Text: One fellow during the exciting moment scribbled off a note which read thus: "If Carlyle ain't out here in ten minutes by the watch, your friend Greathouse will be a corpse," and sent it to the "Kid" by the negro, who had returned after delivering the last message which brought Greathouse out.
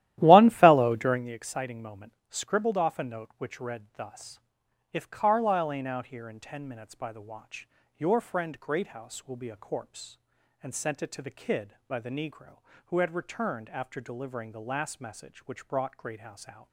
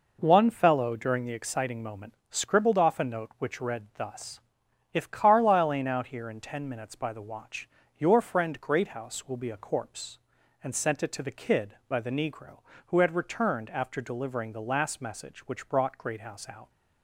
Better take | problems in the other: second | starts louder than the rest; strong; until 1.3 s; 13.5 dB // pauses between "moment" and "scribbled"; slight; at 2.1 s; 0.16 s long; slight in the second

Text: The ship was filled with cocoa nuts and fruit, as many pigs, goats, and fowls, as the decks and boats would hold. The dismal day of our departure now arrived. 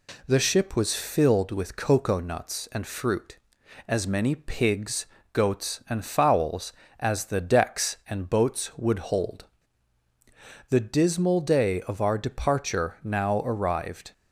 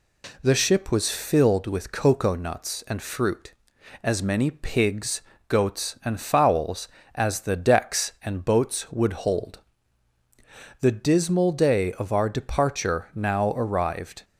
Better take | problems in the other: neither | none

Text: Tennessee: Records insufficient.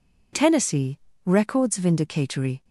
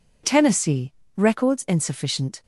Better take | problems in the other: second | says "vindicatory" for "insufficient"; at 1.7 s

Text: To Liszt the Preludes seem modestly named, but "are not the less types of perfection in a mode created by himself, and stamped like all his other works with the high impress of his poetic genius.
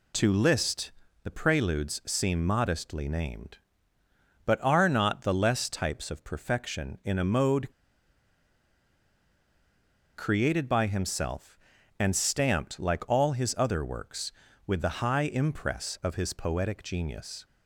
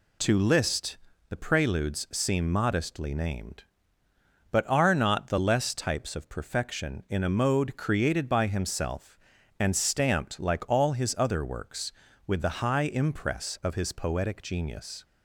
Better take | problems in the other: second | pauses between "Liszt" and "the"; slight; at 0.9 s; 0.32 s long; slight in the second // pauses between "mode" and "created"; strong; at 7.7 s; 2.4 s long

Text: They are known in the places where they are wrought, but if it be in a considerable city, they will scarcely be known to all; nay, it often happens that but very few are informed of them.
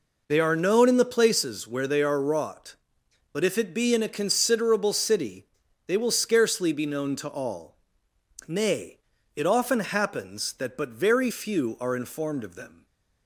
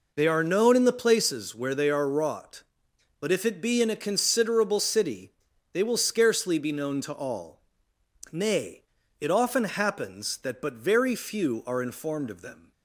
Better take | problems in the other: neither | none

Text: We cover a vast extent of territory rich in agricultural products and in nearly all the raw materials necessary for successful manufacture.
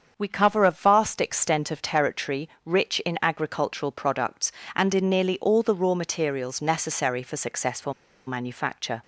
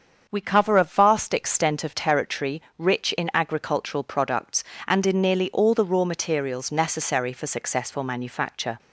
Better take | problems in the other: second | starts louder than the rest; until 1.1 s; 7 dB; also in the second // pauses between "territory" and "rich"; slight; at 2.4 s; 0.16 s long; slight in the second // pauses between "successful" and "manufacture"; slight; at 7.9 s; 0.34 s long

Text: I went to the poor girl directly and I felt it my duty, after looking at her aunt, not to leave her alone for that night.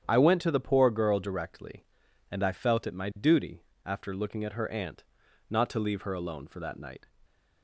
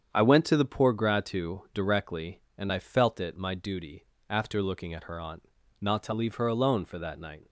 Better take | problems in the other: first | starts louder than the rest; strong; until 1.1 s; 8 dB; strong in the first // says "gratu" for "girl"; at 0.9 s

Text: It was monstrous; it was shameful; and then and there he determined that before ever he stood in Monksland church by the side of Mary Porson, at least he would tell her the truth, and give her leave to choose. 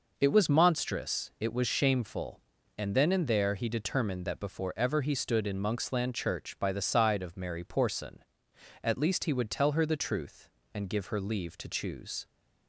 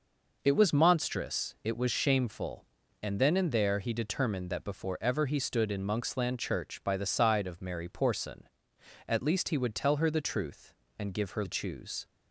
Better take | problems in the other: first | skips "leave to"; at 11.4 s

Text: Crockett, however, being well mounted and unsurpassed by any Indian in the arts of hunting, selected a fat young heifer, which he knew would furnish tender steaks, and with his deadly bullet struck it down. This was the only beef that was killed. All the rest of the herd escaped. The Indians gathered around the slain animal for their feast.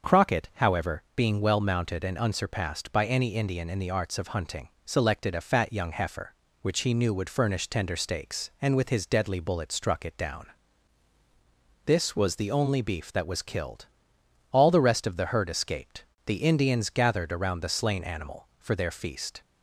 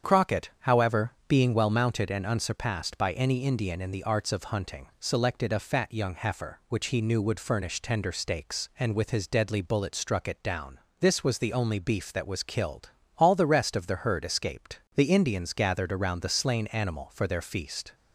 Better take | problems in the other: neither | starts louder than the rest; the same in both

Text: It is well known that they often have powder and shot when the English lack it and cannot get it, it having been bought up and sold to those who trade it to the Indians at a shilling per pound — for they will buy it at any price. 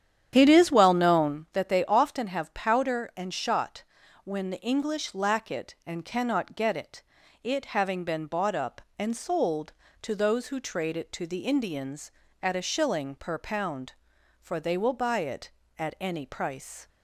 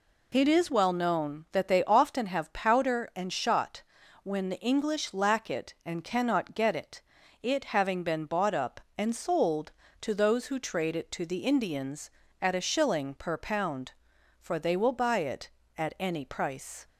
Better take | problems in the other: second | starts louder than the rest; strong; until 1.5 s; 9.5 dB // pauses between "shot" and "when"; at 3.8 s; 0.40 s long; also in the second

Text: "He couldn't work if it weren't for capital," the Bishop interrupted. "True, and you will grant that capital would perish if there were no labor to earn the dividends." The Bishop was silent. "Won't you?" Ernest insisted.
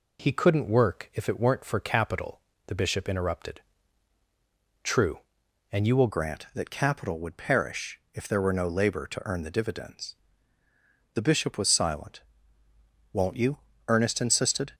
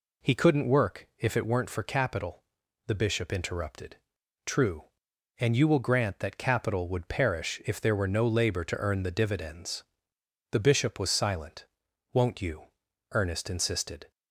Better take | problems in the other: second | changes voice at "grant"; from 6.1 s on; 8.6 s long

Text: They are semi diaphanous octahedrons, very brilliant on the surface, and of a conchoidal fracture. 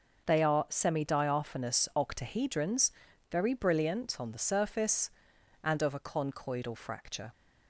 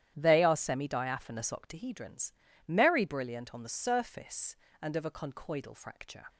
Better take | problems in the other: first | starts louder than the rest; strong; until 1.1 s; 10.5 dB; also in the first // says "merry" for "very"; at 2.6 s

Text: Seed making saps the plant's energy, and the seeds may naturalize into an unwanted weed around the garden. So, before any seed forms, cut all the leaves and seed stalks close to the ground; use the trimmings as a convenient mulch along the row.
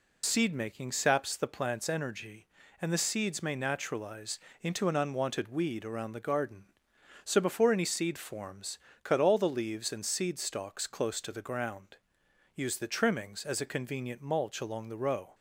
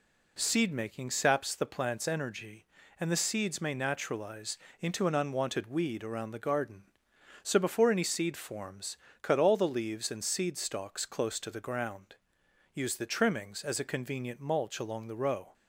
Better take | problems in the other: second | loses the start of "Seed"; at 0.2 s; 60 ms // pauses between "naturalize" and "into"; slight; at 4.4 s; 0.20 s long; slight in the second

